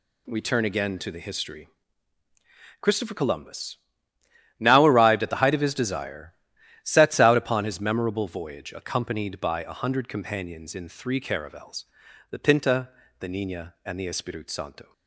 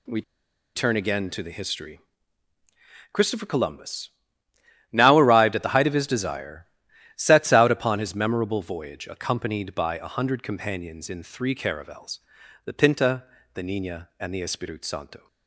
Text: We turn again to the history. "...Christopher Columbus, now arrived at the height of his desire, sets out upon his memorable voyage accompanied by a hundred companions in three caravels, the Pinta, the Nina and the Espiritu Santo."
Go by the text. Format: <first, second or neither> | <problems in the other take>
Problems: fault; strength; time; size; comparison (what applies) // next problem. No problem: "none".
first | pauses between "We" and "turn"; noticeable; at 0.2 s; 0.54 s long